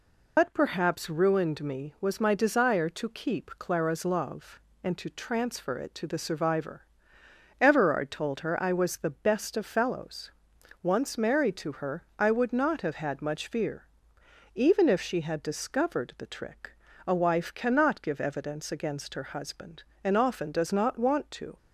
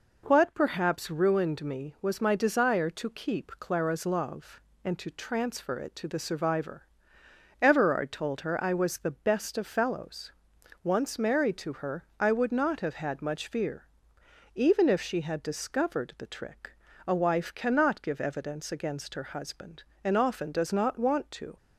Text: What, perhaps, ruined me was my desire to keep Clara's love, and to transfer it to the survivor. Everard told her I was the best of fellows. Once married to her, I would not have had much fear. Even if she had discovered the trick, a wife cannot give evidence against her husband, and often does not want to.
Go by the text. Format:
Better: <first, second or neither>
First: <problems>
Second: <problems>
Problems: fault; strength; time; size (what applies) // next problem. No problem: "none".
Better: second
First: loses the start of "What"; at 0.3 s; 145 ms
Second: none